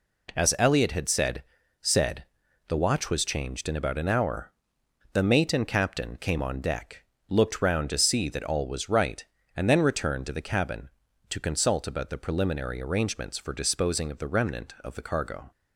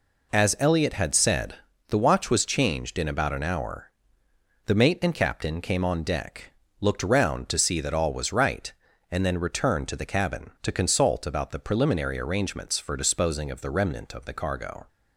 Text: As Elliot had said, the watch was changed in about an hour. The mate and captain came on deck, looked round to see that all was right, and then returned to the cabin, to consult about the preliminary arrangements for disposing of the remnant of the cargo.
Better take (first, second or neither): second